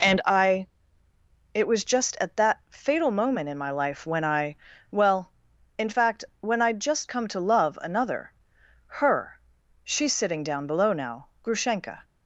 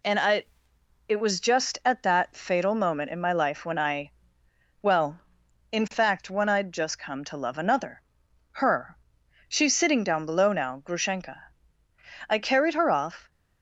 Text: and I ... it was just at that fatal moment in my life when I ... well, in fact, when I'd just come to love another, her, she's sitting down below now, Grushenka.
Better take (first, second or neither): first